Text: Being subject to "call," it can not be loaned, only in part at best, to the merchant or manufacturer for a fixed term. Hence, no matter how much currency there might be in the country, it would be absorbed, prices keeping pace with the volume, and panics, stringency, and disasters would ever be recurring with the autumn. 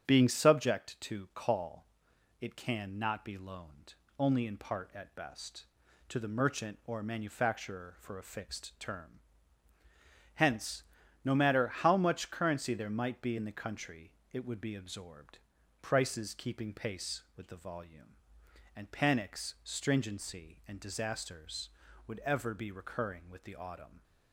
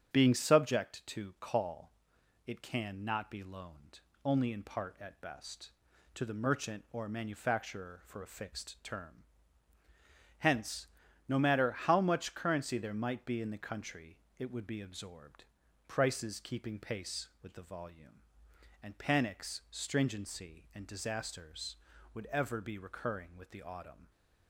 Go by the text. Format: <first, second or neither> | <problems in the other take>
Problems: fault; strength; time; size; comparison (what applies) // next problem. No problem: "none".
neither | starts louder than the rest; strong; the same in both